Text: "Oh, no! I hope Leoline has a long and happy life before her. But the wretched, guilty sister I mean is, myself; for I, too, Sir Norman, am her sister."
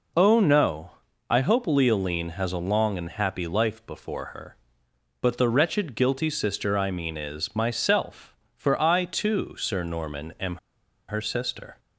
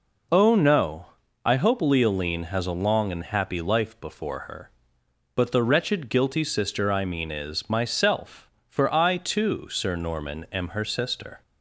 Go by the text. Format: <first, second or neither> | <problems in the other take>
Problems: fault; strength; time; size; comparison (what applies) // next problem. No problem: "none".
second | pauses between "am" and "her"; noticeable; at 10.5 s; 0.50 s long